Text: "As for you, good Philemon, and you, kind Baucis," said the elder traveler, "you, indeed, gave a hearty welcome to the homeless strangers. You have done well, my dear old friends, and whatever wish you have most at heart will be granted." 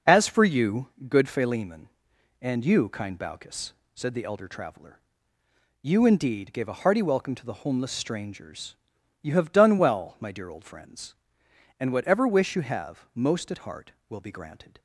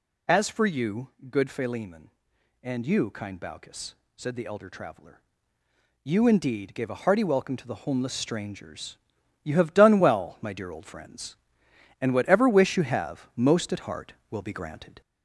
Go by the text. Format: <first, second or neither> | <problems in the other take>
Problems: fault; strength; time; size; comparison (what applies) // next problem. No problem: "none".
first | gets louder; slight; throughout; 2.5 dB